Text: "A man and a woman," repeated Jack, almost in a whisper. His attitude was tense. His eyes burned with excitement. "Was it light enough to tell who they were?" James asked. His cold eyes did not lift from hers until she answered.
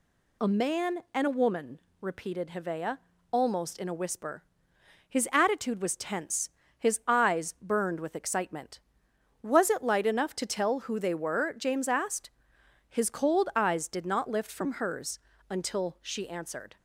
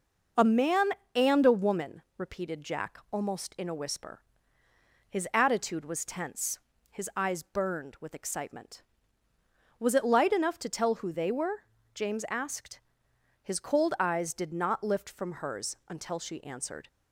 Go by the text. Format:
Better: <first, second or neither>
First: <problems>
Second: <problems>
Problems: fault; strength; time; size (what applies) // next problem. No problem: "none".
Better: second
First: says "Hevea" for "Jack"; at 2.4 s // pauses between "hers" and "until"; slight; at 15.1 s; 0.30 s long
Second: none